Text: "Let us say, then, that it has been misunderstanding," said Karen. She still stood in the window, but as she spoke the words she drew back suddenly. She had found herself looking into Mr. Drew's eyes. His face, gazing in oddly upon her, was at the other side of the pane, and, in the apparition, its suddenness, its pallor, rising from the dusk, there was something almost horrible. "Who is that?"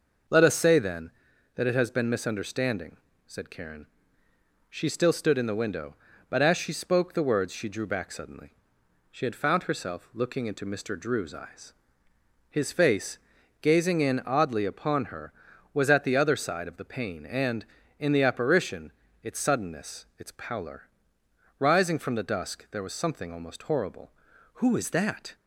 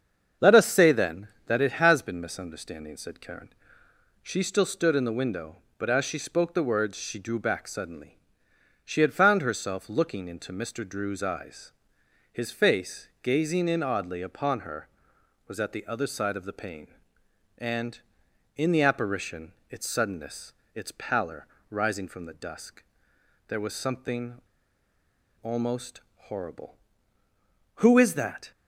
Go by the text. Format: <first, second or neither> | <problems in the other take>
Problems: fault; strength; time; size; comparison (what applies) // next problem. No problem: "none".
first | starts louder than the rest; until 1.5 s; 7 dB // pauses between "something" and "almost"; at 24.4 s; 1.0 s long